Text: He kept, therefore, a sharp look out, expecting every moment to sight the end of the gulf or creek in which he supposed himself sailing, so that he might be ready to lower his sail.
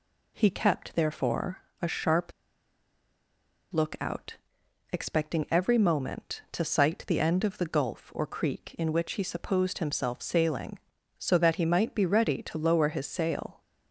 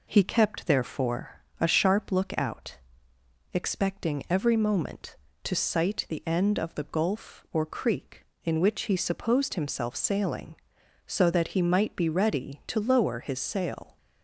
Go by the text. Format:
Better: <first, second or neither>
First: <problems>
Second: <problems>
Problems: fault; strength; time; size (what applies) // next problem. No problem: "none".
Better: second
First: pauses between "sharp" and "look"; strong; at 2.3 s; 1.4 s long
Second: none